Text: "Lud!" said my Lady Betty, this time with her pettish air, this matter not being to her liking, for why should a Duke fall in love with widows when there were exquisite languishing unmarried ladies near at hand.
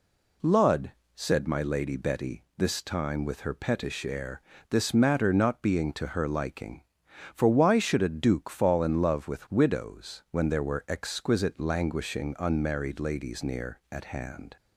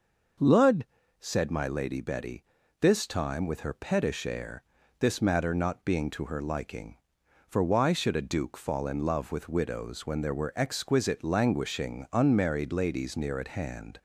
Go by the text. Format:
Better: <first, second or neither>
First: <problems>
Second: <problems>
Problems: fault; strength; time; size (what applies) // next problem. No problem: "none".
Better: neither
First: none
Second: none